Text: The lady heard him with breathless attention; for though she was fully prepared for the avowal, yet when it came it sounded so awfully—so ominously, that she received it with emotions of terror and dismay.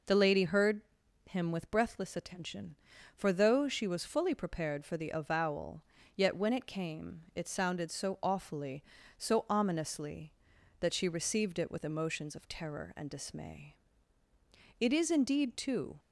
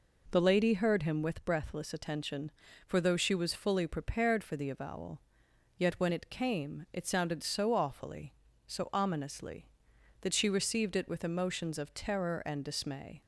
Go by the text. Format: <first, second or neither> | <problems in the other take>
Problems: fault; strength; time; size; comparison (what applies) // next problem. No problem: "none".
second | pauses between "heard" and "him"; noticeable; at 0.8 s; 0.46 s long // goes on to say "It is indeed too"; noticeable; from 14.7 s on; 1.2 s long